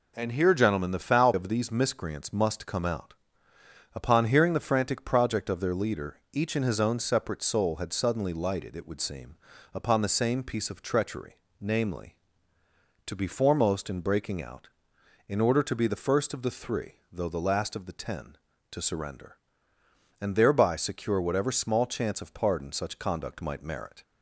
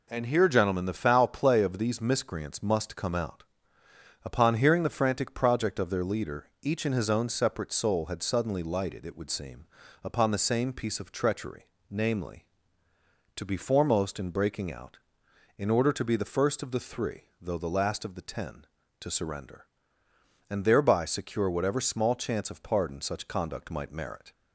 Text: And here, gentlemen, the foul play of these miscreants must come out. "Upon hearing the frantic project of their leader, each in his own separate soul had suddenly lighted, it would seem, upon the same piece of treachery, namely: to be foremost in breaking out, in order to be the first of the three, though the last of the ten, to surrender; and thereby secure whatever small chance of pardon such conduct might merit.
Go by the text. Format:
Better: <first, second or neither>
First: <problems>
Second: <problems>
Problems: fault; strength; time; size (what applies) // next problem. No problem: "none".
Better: second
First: skips "play"; at 1.3 s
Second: none